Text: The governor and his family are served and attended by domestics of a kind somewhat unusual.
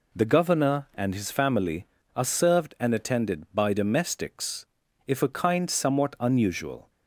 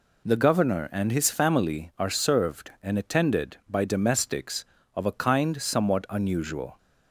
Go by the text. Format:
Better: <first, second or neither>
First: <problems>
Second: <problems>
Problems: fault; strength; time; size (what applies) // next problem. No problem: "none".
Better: second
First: says "if" for "of"; at 5.0 s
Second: none